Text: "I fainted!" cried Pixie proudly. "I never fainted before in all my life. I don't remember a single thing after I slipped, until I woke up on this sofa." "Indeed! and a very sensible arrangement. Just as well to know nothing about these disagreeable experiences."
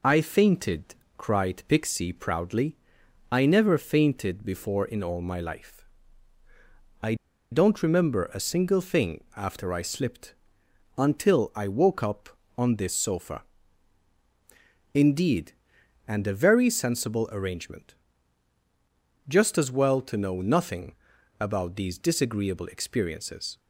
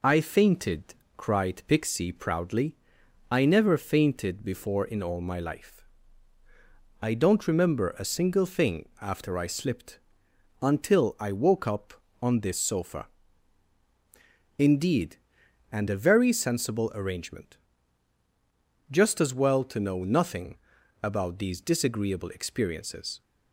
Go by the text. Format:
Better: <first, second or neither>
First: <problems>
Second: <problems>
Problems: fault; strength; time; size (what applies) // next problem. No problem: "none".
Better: second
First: pauses between "I" and "don't"; at 7.1 s; 0.37 s long // pauses between "nothing" and "about"; at 20.9 s; 0.44 s long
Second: pauses between "nothing" and "about"; at 20.5 s; 0.44 s long